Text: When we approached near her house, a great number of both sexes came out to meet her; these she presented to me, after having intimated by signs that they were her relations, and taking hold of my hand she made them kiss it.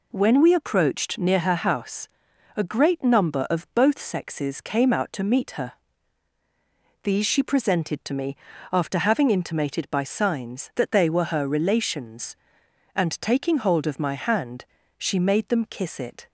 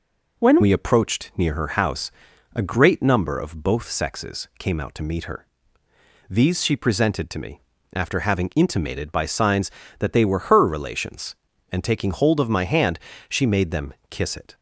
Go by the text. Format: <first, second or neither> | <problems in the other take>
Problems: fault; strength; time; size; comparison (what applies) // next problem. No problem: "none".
first | changes voice at "we"; from 0.6 s on; 13.9 s long // pauses between "hand" and "she"; slight; at 13.0 s; 0.28 s long; slight in the first // pauses between "them" and "kiss"; slight; at 13.9 s; 0.18 s long